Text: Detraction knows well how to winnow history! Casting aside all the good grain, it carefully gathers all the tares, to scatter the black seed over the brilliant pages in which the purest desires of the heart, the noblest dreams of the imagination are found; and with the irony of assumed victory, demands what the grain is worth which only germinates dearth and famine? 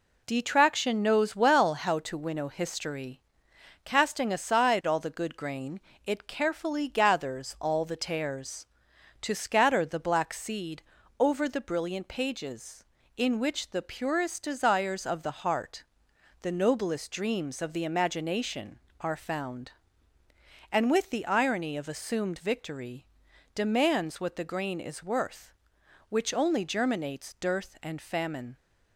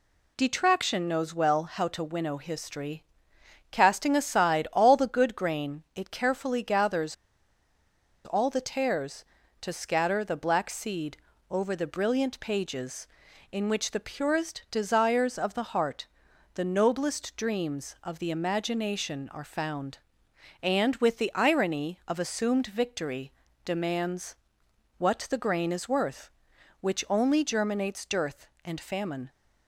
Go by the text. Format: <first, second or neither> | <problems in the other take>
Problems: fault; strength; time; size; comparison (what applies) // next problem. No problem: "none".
first | pauses between "gathers" and "all"; at 7.1 s; 1.1 s long // pauses between "seed" and "over"; slight; at 11.1 s; 0.32 s long; also in the first // pauses between "demands" and "what"; noticeable; at 24.3 s; 0.62 s long